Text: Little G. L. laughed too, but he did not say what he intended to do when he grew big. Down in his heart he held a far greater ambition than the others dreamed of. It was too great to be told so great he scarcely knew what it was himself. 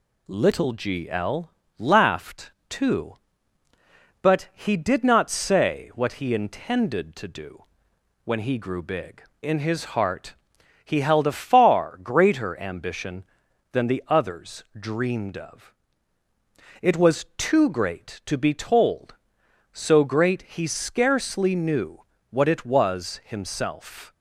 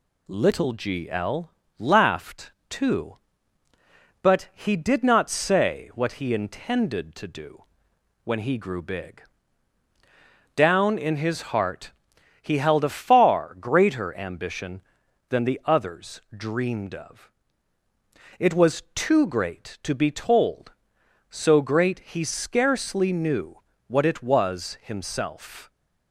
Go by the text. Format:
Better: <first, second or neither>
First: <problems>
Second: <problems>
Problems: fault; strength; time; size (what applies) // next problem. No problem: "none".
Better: second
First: pauses between "L" and "laughed"; slight; at 1.5 s; 0.28 s long // pauses between "laughed" and "too"; slight; at 2.5 s; 0.20 s long // pauses between "do" and "when"; noticeable; at 7.6 s; 0.60 s long // skips "Down"; at 9.3 s // pauses between "heart" and "he"; noticeable; at 10.3 s; 0.50 s long // pauses between "knew" and "what"; slight; at 22.0 s; 0.28 s long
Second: pauses between "L" and "laughed"; slight; at 1.5 s; 0.28 s long // pauses between "laughed" and "too"; slight; at 2.5 s; 0.20 s long // pauses between "do" and "when"; noticeable; at 7.6 s; 0.60 s long // pauses between "heart" and "he"; noticeable; at 11.9 s; 0.50 s long // pauses between "knew" and "what"; slight; at 23.5 s; 0.28 s long